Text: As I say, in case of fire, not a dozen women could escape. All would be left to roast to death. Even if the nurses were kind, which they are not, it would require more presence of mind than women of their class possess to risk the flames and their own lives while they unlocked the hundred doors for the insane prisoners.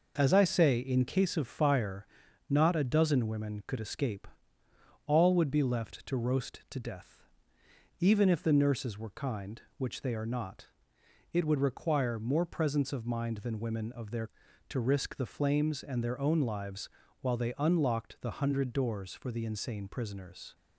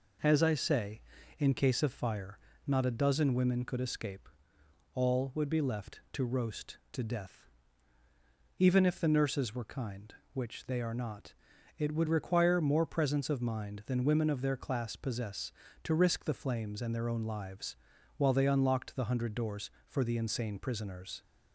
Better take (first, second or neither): second